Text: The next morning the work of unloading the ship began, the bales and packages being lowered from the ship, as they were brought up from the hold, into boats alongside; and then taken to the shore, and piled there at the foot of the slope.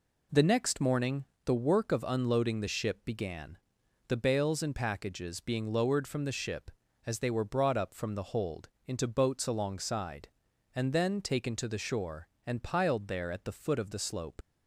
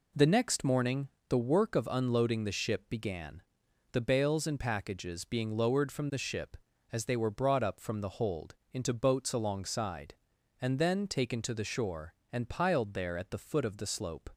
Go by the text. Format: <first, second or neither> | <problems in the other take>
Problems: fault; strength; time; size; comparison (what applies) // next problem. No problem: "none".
second | pauses between "morning" and "the"; slight; at 1.2 s; 0.22 s long; slight in the second // leaves "slope" unfinished; at 14.4 s; 55 ms